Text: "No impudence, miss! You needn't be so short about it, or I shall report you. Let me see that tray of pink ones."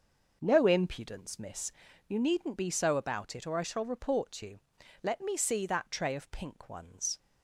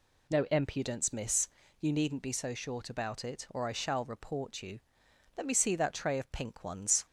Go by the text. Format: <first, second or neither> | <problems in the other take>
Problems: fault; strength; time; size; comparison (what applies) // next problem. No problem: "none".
second | skips "short"; at 2.9 s